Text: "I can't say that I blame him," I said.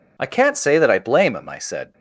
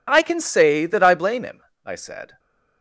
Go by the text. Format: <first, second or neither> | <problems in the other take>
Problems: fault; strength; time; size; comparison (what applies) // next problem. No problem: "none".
first | says "can" for "can't"; at 0.2 s